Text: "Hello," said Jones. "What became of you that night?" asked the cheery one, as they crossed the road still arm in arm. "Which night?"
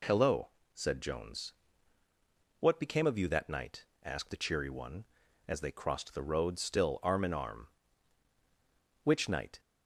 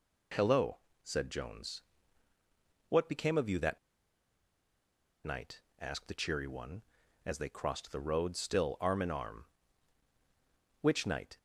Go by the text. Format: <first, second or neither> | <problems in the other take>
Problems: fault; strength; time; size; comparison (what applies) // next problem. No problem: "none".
first | pauses between "that" and "night"; strong; at 3.7 s; 1.4 s long